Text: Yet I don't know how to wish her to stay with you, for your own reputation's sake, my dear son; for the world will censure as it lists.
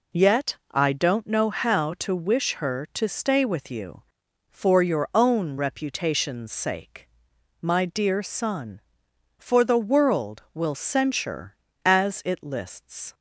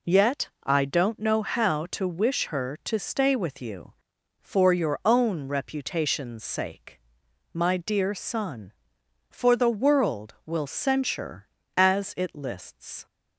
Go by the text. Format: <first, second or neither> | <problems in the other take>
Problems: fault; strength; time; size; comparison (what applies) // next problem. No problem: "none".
neither | none